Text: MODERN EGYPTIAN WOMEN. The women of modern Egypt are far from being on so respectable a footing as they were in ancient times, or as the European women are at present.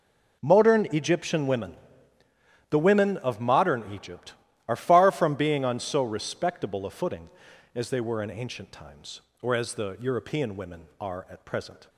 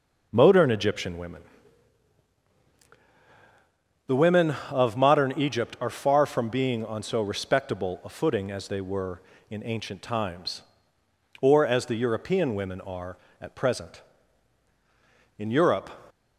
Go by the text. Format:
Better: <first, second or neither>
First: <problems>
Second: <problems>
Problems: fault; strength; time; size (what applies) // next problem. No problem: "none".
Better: first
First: none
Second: goes on to say "In Europe"; from 15.3 s on; 0.50 s long